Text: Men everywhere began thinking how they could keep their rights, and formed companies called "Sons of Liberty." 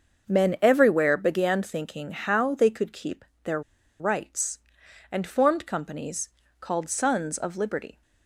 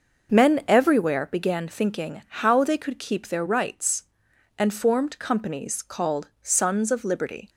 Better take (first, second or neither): second